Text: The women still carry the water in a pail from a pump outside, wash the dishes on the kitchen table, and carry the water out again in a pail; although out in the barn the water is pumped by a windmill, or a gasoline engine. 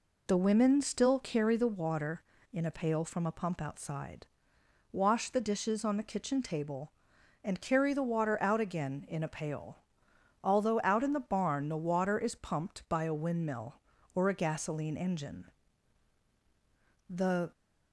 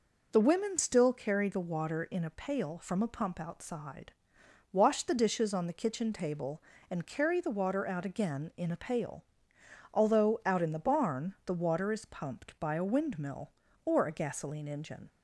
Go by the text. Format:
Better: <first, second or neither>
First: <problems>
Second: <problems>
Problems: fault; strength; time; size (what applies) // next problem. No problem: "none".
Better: second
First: goes on to say "The"; slight; from 17.0 s on; 0.44 s long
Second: none